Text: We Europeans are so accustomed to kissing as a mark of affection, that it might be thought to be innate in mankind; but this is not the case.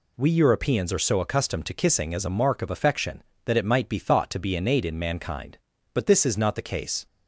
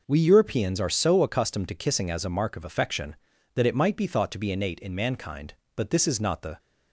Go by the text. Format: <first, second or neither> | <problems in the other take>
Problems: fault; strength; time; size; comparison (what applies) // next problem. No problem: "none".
first | stops before "case"; at 6.5 s